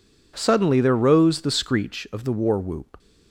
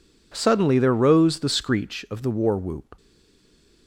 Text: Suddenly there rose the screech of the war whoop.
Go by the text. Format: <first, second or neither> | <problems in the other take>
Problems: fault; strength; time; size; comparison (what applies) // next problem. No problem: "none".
first | stays silent after the last word; slight; from 2.9 s on; 0.9 s long